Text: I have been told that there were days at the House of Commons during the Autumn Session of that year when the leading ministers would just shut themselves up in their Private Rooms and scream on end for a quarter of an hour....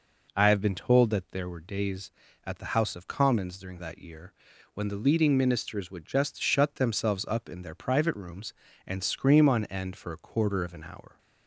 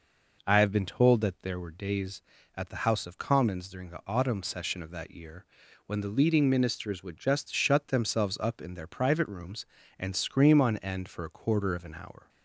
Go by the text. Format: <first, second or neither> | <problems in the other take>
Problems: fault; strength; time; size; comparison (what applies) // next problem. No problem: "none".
second | skips "the Autumn Session of"; at 3.7 s // pauses between "year" and "when"; at 4.3 s; 0.42 s long; also in the second